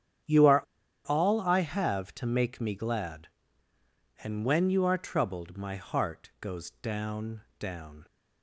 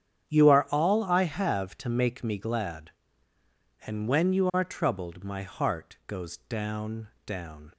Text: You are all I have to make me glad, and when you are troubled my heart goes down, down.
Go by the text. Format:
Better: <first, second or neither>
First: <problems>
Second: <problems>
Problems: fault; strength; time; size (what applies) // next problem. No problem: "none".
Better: second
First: starts louder than the rest; strong; until 1.7 s; 9 dB // pauses between "are" and "all"; at 0.6 s; 0.45 s long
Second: starts louder than the rest; strong; until 1.3 s; 9.5 dB